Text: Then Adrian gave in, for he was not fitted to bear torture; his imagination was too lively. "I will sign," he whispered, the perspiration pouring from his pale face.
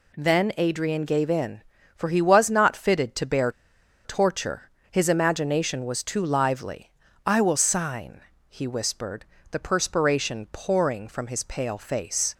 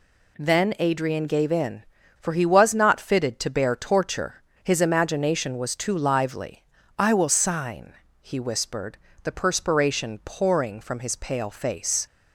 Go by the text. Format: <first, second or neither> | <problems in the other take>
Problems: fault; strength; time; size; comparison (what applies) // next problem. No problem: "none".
second | pauses between "bear" and "torture"; noticeable; at 3.5 s; 0.53 s long